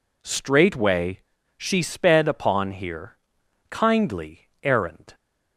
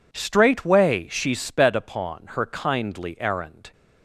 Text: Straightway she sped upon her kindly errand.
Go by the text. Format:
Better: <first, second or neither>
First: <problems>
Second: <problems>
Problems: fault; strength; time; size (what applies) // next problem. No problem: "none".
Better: second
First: pauses between "Straightway" and "she"; slight; at 1.2 s; 0.36 s long // says "here" for "her"; at 2.7 s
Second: none